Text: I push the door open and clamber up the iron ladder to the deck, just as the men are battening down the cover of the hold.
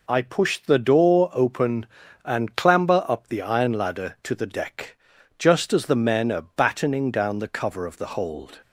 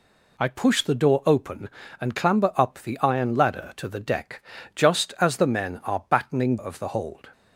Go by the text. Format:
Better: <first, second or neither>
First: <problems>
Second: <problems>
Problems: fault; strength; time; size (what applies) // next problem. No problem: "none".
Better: first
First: none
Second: skips "down the cover"; at 6.5 s